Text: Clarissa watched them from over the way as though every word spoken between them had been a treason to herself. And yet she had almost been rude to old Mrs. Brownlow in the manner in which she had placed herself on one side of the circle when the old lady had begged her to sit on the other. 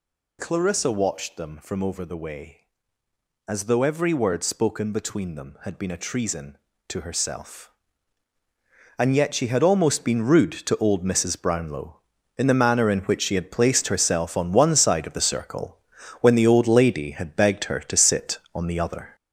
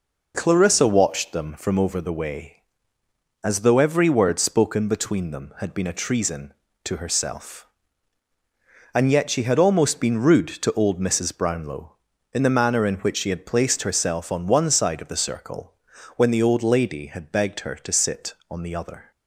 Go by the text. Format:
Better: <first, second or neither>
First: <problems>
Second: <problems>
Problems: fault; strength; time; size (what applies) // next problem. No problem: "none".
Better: second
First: gets louder; throughout; 6.5 dB // pauses between "circle" and "when"; at 15.7 s; 0.44 s long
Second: pauses between "circle" and "when"; at 15.7 s; 0.44 s long